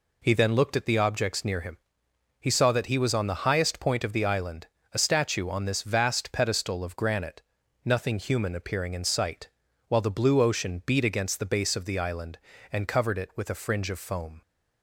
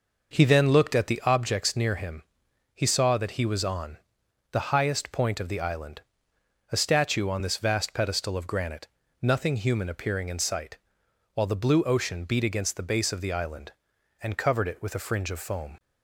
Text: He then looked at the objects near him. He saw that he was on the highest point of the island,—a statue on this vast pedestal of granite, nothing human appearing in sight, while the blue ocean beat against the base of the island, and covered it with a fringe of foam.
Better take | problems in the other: first | starts louder than the rest; noticeable; until 1.4 s; 6 dB // pauses between "on" and "the"; noticeable; at 3.9 s; 0.54 s long

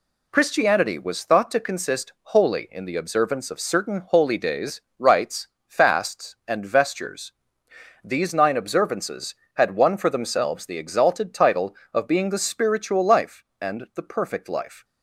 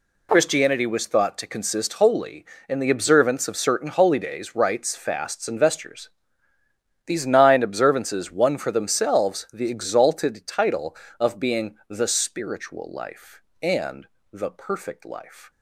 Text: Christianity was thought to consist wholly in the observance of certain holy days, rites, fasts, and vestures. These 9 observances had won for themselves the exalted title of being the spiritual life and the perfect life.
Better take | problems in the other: first | skips "had"; at 8.2 s // pauses between "and" and "the"; slight; at 14.0 s; 0.26 s long

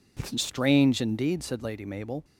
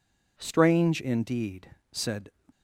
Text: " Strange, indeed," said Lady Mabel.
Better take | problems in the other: first | stops before "Lady Mabel"; at 2.5 s

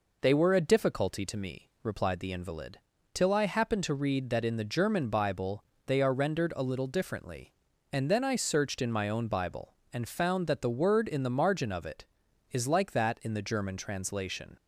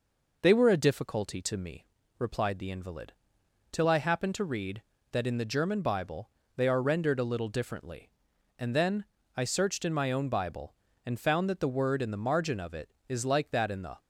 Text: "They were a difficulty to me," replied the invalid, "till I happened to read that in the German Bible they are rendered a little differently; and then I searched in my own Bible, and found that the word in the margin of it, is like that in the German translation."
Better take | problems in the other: first | pauses between "Bible" and "they"; slight; at 6.2 s; 0.28 s long; slight in the first // pauses between "then" and "I"; slight; at 9.0 s; 0.32 s long // stops before "German translation"; at 13.9 s

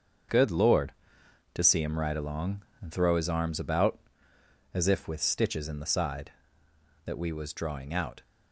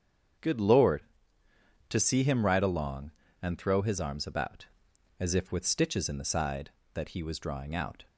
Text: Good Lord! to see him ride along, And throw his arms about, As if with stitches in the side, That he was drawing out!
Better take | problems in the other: second | starts louder than the rest; until 1.9 s; 6.5 dB; strong in the second // says "we" for "he"; at 7.1 s

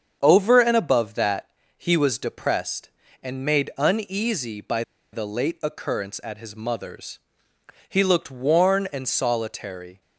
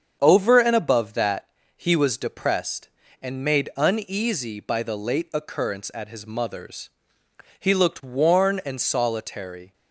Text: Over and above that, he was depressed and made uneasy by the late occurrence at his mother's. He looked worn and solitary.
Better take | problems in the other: second | starts louder than the rest; strong; until 1.2 s; 7.5 dB; strong in the second // pauses between "by" and "the"; slight; at 4.8 s; 0.31 s long

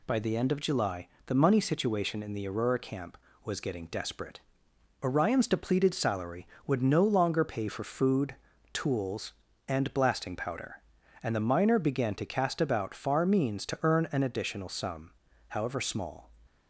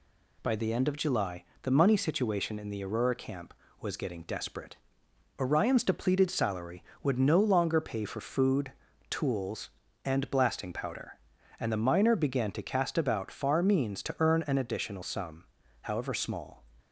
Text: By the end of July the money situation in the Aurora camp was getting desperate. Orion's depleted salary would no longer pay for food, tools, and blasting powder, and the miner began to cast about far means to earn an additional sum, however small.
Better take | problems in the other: neither | pauses between "July" and "the"; slight; the same in both

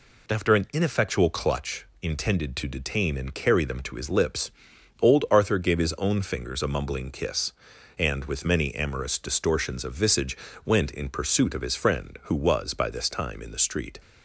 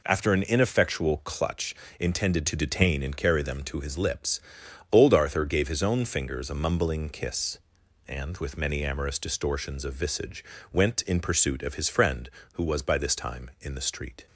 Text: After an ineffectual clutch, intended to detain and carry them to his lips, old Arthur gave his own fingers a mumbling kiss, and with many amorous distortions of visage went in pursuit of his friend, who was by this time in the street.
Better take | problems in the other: neither | pauses between "visage" and "went"; slight; the same in both

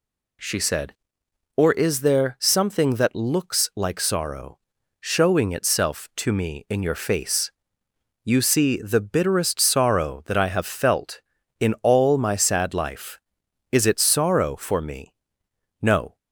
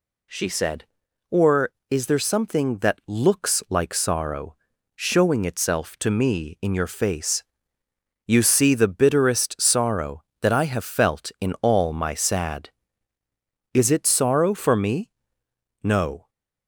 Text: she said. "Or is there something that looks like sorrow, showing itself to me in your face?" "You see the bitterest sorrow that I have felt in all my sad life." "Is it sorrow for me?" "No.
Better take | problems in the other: first | skips "life"; at 13.2 s

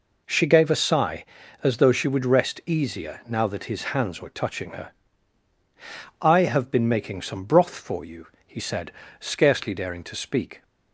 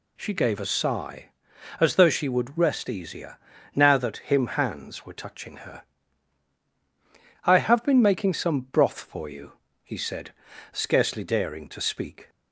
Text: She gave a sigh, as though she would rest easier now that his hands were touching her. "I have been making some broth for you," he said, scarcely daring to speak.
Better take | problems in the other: first | pauses between "easier" and "now"; at 3.3 s; 0.38 s long // says "him" for "his"; at 4.1 s

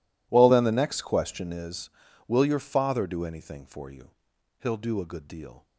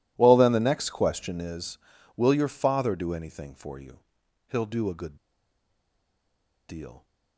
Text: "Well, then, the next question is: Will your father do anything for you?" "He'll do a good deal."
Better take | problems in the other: first | pauses between "good" and "deal"; strong; at 5.1 s; 1.5 s long

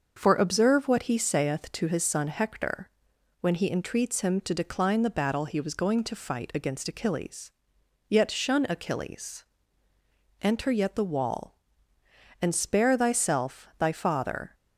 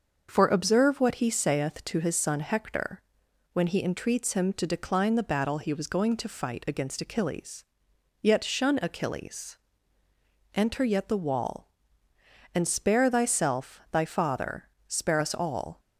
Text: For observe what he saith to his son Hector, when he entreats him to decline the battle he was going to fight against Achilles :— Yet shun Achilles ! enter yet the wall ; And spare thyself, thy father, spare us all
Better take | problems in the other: second | starts louder than the rest; until 1.1 s; 6.5 dB; also in the second // stops before "spare us all"; at 14.5 s

